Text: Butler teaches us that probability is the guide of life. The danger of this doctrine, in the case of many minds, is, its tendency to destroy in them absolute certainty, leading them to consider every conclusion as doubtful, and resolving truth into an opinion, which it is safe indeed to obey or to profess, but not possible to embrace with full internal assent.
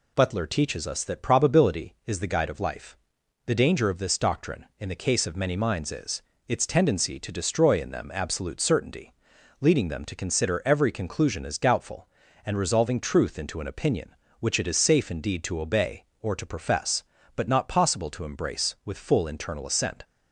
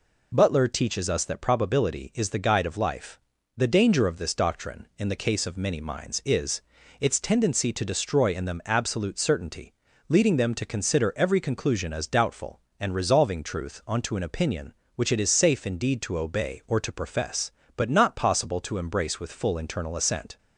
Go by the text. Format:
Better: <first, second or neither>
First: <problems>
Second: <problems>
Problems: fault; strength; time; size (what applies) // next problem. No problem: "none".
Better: first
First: none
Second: says "onto" for "into"; at 13.8 s